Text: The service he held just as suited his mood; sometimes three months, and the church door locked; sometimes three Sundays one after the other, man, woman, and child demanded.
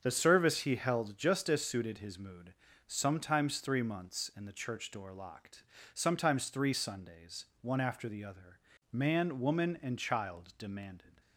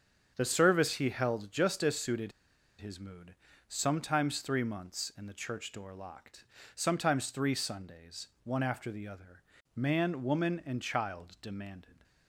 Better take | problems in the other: first | starts louder than the rest; strong; until 1.3 s; 7.5 dB; also in the first // pauses between "suited" and "his"; noticeable; at 2.3 s; 0.47 s long // pauses between "Sundays" and "one"; slight; at 8.2 s; 0.16 s long; slight in the first

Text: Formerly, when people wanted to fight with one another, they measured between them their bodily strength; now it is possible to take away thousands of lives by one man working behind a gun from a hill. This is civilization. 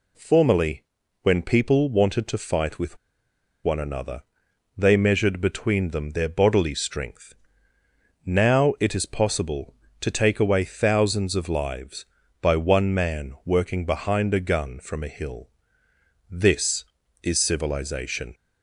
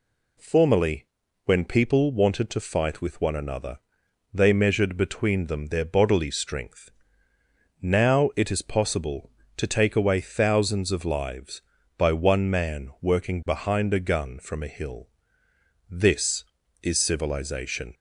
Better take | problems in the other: second | pauses between "with" and "one"; noticeable; at 2.9 s; 0.66 s long

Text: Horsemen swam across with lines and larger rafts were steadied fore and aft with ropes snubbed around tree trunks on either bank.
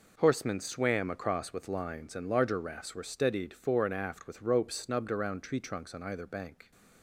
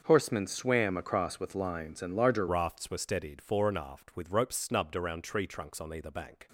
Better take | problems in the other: first | starts louder than the rest; until 1.0 s; 6.5 dB // changes voice at "rafts"; from 2.4 s on; 4.0 s long

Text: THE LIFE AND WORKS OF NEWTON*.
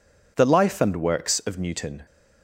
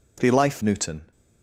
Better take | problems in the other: first | skips "AND WORKS OF"; at 0.6 s

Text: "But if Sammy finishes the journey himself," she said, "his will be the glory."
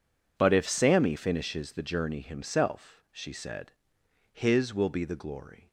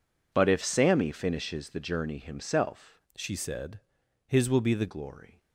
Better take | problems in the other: first | changes voice from "she" to "the"; from 3.1 to 4.8 s; 1.7 s long

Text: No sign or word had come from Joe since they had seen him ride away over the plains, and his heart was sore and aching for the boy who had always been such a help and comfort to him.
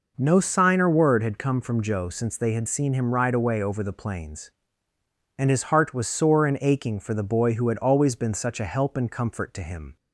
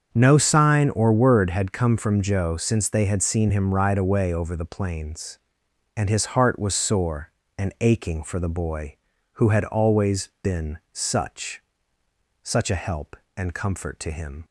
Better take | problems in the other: first | starts louder than the rest; strong; until 1.1 s; 7 dB // says "such" twice; at 12.4 s

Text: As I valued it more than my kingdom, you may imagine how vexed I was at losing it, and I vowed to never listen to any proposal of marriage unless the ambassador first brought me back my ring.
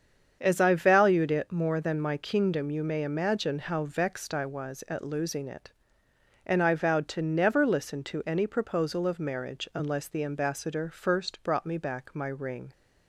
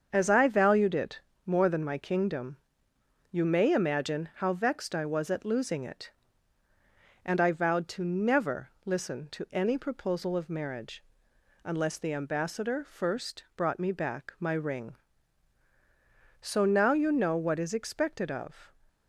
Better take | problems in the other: first | starts louder than the rest; until 1.1 s; 7 dB; strong in the first // pauses between "it" and "more"; slight; at 1.2 s; 0.26 s long // pauses between "marriage" and "unless"; noticeable; at 11.0 s; 0.58 s long // goes on to say "So now you know what is expected of"; strong; from 16.4 s on; 2.3 s long

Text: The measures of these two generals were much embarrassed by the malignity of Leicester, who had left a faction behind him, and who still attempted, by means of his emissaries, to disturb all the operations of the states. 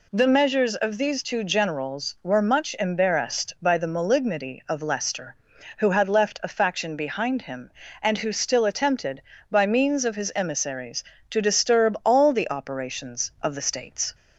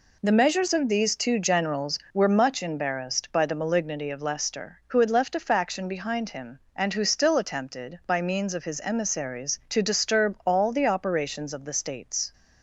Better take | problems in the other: neither | none

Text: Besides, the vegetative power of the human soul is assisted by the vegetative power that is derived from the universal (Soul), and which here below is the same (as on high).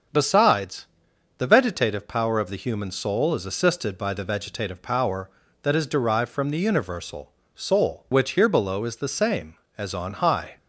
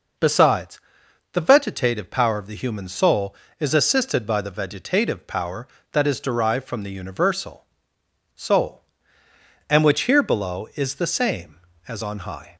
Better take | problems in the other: second | starts louder than the rest; until 1.6 s; 6.5 dB // skips "and"; at 8.0 s

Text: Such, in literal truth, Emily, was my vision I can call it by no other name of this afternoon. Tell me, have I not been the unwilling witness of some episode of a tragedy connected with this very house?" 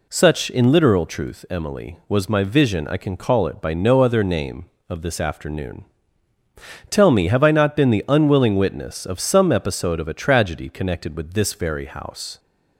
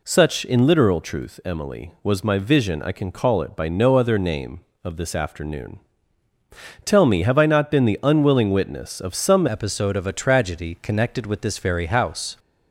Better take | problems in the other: first | changes voice at "episode"; from 9.4 s on; 2.9 s long

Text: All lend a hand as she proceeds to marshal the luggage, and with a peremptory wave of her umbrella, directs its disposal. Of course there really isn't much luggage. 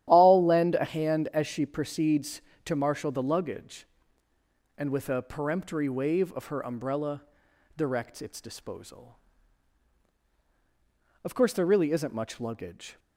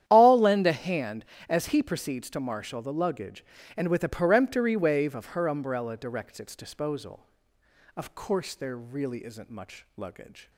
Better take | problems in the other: first | starts louder than the rest; strong; until 1.0 s; 10.5 dB; strong in the first // says "he" for "she"; at 1.6 s

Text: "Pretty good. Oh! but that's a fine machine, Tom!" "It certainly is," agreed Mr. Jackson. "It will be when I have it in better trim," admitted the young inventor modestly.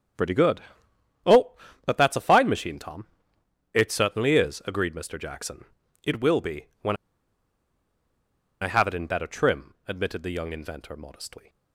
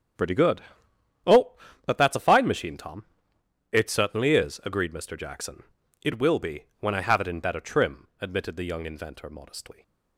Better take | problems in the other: second | starts louder than the rest; strong; until 2.1 s; 8 dB; strong in the second // pauses between "when" and "I"; strong; at 6.9 s; 1.6 s long

